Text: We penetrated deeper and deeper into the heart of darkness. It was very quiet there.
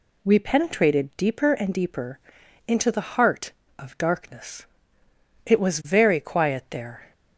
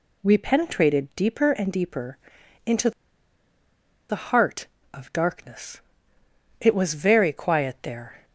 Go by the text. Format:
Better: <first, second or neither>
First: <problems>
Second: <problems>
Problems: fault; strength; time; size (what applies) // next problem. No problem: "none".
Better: first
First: pauses between "deeper" and "into"; noticeable; at 2.1 s; 0.48 s long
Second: pauses between "deeper" and "into"; noticeable; at 2.1 s; 0.48 s long // pauses between "into" and "the"; at 2.9 s; 1.1 s long